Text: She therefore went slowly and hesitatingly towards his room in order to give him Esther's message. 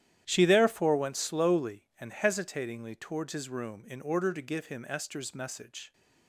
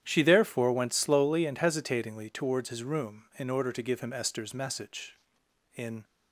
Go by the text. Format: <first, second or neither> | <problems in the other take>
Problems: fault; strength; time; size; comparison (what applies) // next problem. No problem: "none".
first | starts louder than the rest; strong; until 1.0 s; 10.5 dB; strong in the first // goes on to say "In"; slight; from 5.7 s on; 0.28 s long